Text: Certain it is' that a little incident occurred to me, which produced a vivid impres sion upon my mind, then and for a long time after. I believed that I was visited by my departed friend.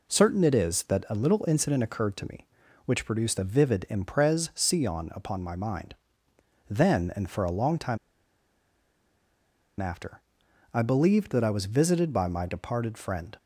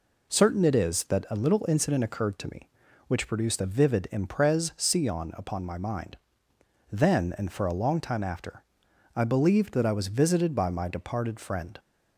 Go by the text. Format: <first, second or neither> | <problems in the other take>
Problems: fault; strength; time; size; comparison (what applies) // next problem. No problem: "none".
second | pauses between "time" and "after"; strong; at 7.9 s; 1.8 s long